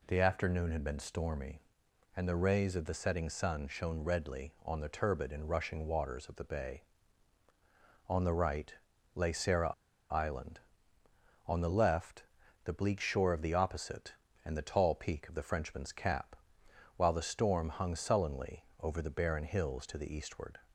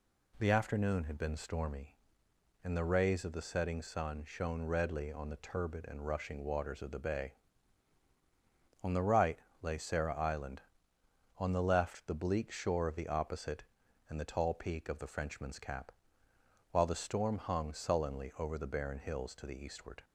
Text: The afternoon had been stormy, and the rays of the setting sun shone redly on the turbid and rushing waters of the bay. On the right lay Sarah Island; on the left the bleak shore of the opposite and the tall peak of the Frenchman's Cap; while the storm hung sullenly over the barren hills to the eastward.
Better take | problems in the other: second | pauses between "right" and "lay"; at 8.7 s; 0.42 s long; slight in the second // pauses between "Sarah" and "Island"; at 9.7 s; 0.39 s long // pauses between "left" and "the"; at 12.2 s; 0.40 s long

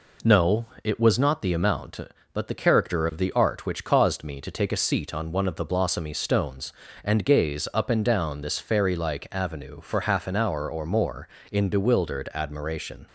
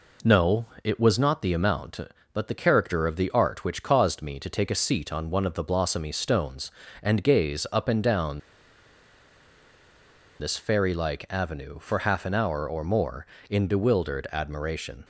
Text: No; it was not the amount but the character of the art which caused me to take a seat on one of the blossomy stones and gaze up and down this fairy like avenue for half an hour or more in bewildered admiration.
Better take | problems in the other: first | pauses between "down" and "this"; strong; at 8.3 s; 2.0 s long

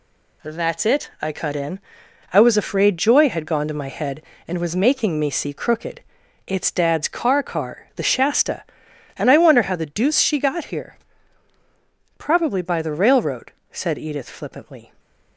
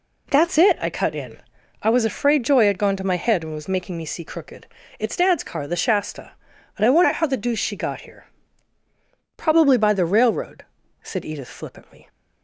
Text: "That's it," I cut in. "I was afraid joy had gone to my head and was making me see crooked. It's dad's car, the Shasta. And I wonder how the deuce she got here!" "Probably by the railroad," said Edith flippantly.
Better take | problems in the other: second | says "car" twice; at 7.4 s

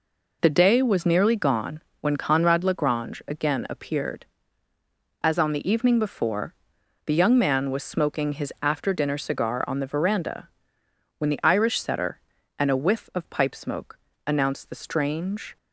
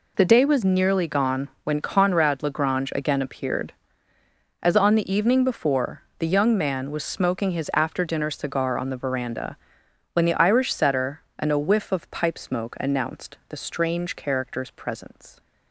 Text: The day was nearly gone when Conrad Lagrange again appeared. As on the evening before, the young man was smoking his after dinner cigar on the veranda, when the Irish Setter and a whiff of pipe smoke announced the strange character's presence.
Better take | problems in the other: second | pauses between "gone" and "when"; slight; at 1.8 s; 0.18 s long; slight in the second // pauses between "smoke" and "announced"; slight; at 13.9 s; 0.26 s long // stops before "character's presence"; at 15.5 s

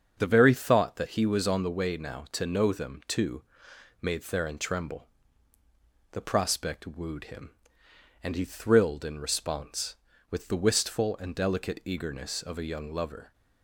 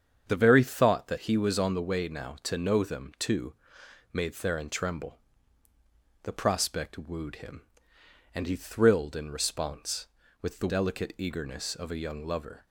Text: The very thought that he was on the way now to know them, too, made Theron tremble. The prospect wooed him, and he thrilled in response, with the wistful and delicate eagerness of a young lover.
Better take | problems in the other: first | starts louder than the rest; strong; until 1.2 s; 7.5 dB; also in the first // skips "wistful and"; at 10.6 s

